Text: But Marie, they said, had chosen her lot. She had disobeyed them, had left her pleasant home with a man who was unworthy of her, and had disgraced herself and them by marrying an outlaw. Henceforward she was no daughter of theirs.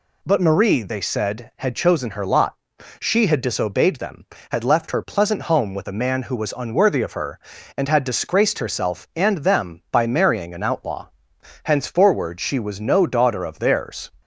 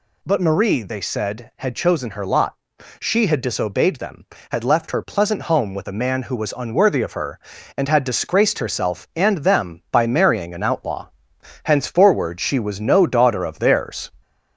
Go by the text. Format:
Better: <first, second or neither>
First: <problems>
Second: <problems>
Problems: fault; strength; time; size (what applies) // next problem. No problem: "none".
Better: first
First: none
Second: gets louder; slight; throughout; 2 dB